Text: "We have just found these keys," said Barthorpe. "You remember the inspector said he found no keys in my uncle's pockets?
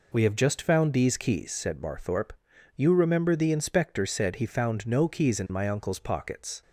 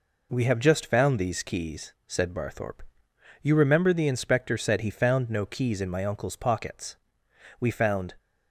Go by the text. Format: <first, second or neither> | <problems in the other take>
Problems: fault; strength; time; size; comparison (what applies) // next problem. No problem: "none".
first | goes on to say "We found"; from 7.5 s on; 0.54 s long